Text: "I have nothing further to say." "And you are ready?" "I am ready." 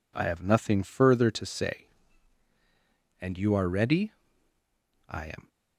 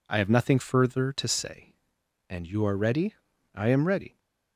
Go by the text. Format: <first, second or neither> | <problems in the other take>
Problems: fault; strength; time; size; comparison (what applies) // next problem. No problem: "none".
second | stops before "ready"; at 5.4 s